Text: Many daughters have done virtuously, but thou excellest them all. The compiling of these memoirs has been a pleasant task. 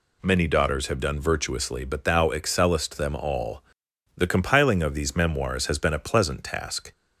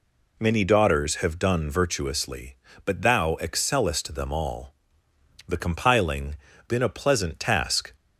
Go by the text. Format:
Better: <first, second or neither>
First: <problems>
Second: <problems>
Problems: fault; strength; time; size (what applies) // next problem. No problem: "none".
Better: first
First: none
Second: skips "of these memoirs has"; at 6.5 s